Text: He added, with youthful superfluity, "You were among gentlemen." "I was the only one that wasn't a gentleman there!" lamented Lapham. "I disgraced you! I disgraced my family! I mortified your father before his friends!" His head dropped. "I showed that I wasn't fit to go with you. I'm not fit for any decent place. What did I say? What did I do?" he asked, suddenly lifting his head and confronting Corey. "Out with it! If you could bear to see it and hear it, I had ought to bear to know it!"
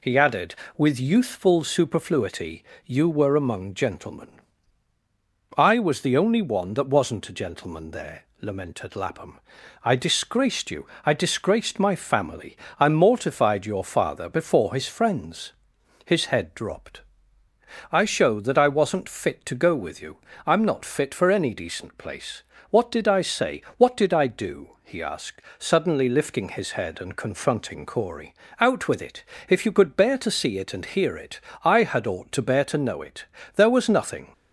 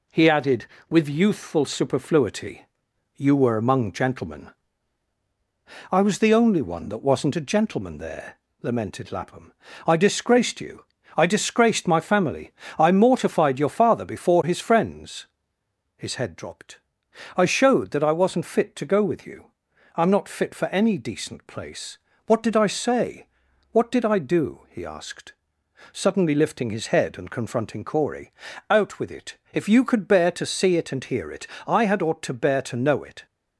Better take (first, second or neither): second